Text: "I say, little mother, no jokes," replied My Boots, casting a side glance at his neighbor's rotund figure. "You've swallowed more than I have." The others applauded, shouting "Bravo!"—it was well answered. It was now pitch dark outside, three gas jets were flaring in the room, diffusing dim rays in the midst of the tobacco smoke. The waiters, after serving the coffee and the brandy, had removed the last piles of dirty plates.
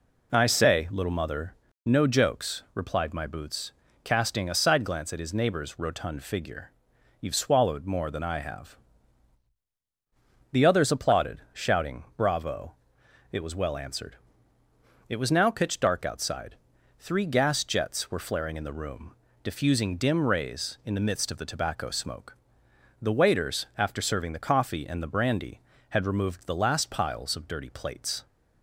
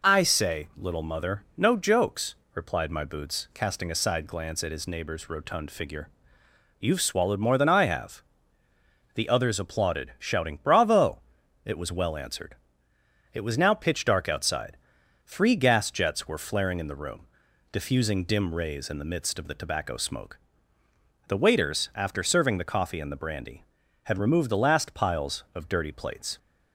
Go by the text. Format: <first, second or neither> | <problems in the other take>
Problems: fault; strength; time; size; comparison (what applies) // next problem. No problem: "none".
neither | none